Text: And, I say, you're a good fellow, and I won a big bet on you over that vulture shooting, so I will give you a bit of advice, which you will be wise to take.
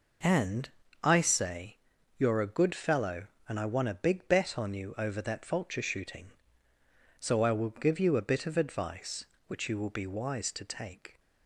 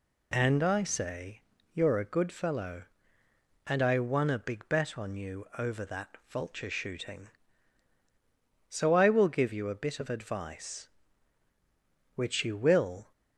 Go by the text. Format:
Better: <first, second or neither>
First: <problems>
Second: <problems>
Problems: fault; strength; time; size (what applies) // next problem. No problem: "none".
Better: first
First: none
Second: stops before "be wise to take"; at 13.1 s